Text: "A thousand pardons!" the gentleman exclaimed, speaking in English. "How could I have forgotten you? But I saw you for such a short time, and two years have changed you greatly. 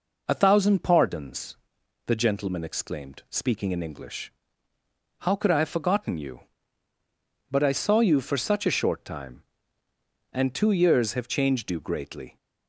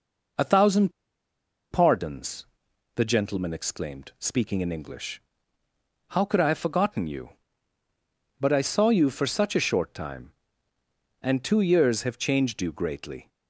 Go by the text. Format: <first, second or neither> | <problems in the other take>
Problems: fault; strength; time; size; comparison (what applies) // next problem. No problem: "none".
first | pauses between "thousand" and "pardons"; noticeable; at 0.9 s; 0.80 s long